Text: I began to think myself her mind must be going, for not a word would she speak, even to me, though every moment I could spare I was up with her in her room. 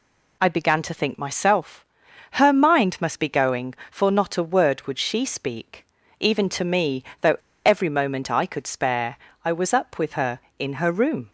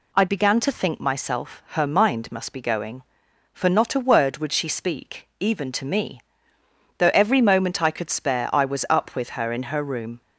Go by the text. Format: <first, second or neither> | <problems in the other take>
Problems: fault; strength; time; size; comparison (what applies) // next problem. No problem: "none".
second | pauses between "myself" and "her"; noticeable; at 1.8 s; 0.46 s long // pauses between "though" and "every"; slight; at 7.3 s; 0.27 s long // pauses between "spare" and "I"; slight; at 9.1 s; 0.30 s long